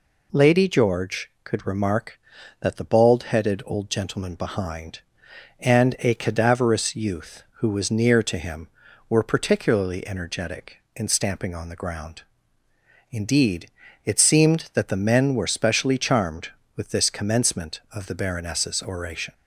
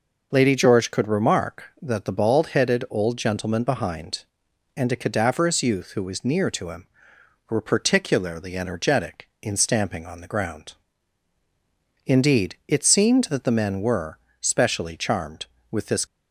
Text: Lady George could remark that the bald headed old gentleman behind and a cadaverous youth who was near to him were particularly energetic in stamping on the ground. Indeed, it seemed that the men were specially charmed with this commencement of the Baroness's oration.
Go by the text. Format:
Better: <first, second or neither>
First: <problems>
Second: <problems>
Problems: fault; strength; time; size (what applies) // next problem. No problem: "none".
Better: first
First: none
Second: pauses between "were" and "specially"; slight; at 14.1 s; 0.22 s long // stops before "commencement of the Baroness's oration"; at 16.0 s